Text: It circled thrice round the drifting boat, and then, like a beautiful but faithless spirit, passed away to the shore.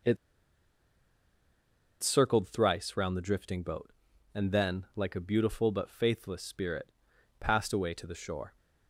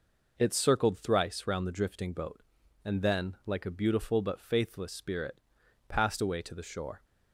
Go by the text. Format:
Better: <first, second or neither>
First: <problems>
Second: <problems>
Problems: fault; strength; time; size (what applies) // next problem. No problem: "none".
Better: second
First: pauses between "It" and "circled"; strong; at 0.1 s; 1.8 s long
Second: none